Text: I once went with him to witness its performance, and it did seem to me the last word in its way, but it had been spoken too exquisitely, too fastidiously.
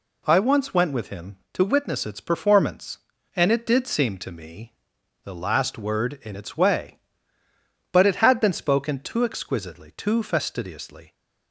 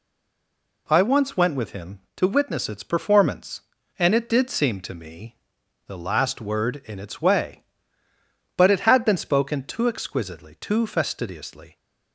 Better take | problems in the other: first | stays silent before the first word; slight; until 0.8 s; 0.8 s long // pauses between "me" and "the"; noticeable; at 5.3 s; 0.52 s long; noticeable in the first

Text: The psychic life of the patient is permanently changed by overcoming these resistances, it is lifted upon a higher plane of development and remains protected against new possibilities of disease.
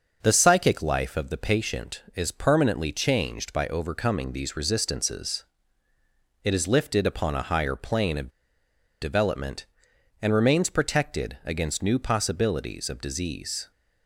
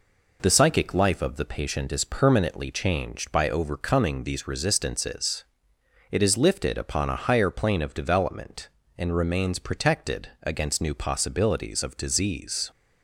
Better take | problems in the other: second | starts louder than the rest; until 1.2 s; 6 dB // pauses between "of" and "development"; noticeable; at 8.2 s; 0.73 s long

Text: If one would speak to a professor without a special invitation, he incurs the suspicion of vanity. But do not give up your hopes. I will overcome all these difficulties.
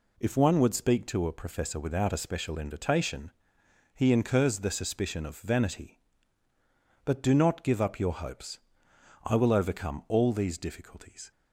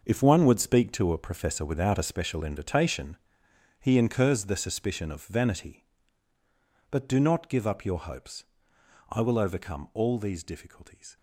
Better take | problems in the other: first | gets quieter; strong; throughout; 10.5 dB

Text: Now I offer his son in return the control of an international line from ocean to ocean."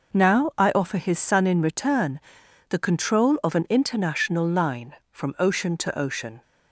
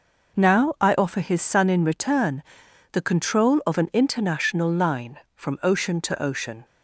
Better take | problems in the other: neither | pauses between "return" and "the"; noticeable; the same in both

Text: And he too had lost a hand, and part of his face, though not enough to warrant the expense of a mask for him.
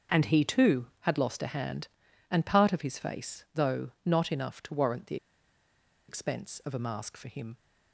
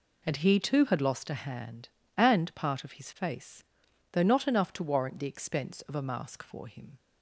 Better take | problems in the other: second | starts louder than the rest; until 1.2 s; 6.5 dB // pauses between "the" and "expense"; noticeable; at 5.1 s; 0.92 s long

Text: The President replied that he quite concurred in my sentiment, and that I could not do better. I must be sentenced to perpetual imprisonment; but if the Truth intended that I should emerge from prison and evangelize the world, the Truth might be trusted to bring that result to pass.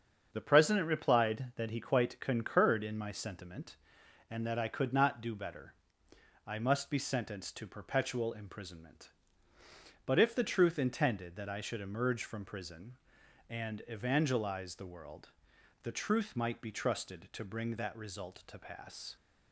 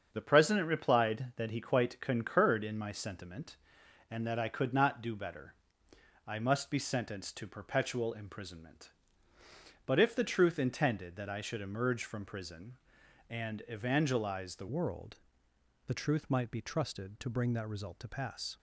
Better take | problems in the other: first | starts louder than the rest; strong; until 1.1 s; 7 dB; strong in the first // changes voice at "world"; from 14.6 s on; 3.9 s long

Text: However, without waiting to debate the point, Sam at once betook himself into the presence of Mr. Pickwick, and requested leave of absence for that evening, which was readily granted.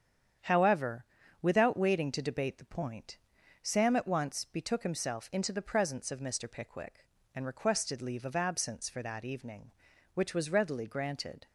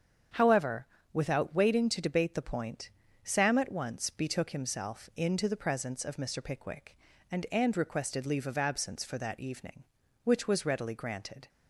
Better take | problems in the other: first | starts louder than the rest; strong; until 1.5 s; 7.5 dB; strong in the first // says "and" twice; at 7.5 s

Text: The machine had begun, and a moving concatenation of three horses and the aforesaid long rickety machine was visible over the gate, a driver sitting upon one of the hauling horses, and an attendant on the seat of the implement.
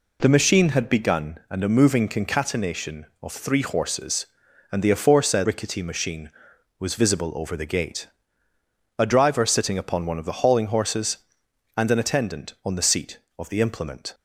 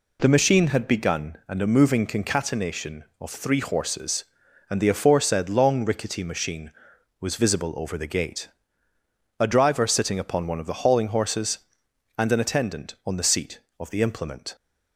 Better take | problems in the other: second | skips "long"; at 5.4 s

